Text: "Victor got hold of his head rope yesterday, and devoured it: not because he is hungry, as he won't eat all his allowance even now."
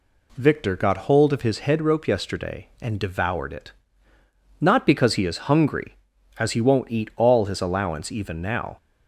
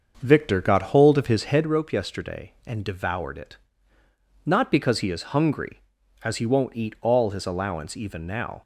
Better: first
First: none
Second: starts louder than the rest; until 1.8 s; 6.5 dB

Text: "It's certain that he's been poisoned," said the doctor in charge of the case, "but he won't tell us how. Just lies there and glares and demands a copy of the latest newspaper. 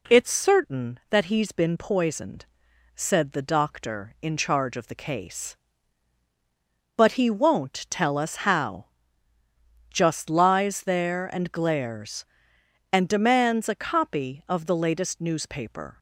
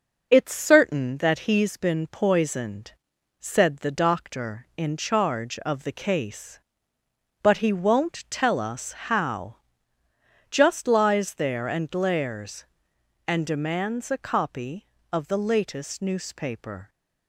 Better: first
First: none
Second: gets quieter; slight; throughout; 3.5 dB

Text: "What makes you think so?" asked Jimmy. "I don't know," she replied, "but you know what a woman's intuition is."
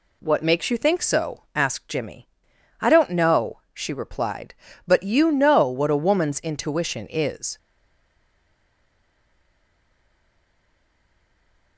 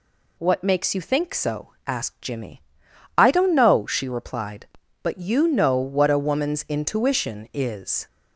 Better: second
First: stays silent after the last word; strong; from 7.5 s on; 4.2 s long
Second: none

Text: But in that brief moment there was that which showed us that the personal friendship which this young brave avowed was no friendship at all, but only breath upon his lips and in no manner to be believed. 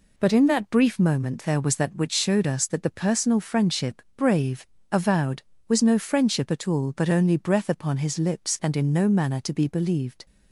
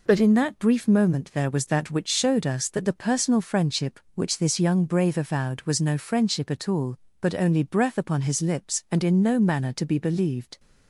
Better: second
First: skips "which this young"; at 4.0 s // pauses between "brave" and "avowed"; slight; at 4.6 s; 0.28 s long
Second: none

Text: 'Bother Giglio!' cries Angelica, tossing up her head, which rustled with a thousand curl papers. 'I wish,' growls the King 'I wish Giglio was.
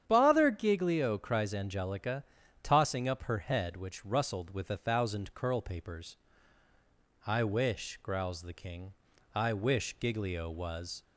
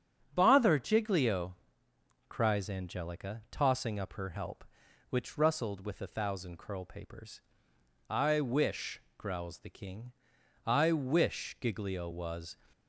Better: first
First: starts louder than the rest; strong; until 1.0 s; 9 dB // pauses between "King" and "I"; at 8.9 s; 0.42 s long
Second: starts louder than the rest; strong; until 1.3 s; 8 dB // says "help" for "head"; at 4.2 s // pauses between "King" and "I"; noticeable; at 10.1 s; 0.52 s long

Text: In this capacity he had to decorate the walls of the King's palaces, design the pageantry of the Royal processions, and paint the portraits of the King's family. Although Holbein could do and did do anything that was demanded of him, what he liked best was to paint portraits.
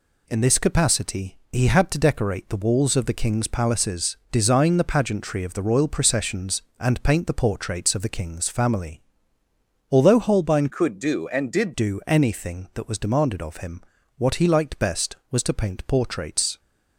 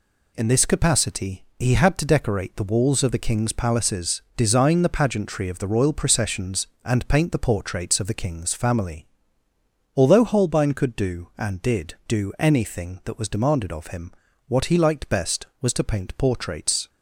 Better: second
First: changes voice from "could" to "did"; from 10.6 to 11.7 s; 1.1 s long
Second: none

